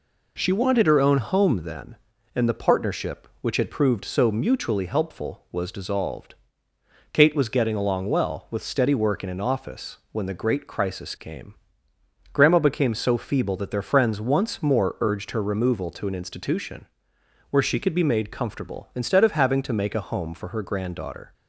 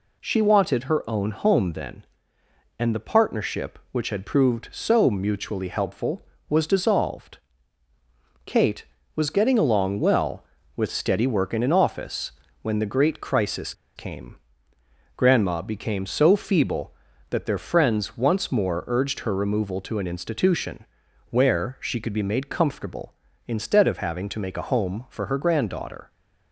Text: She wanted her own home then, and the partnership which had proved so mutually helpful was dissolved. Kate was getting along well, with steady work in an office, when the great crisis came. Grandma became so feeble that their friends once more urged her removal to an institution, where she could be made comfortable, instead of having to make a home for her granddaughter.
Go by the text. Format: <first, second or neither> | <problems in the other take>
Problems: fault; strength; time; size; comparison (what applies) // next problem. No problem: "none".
first | pauses between "crisis" and "came"; slight; at 13.7 s; 0.23 s long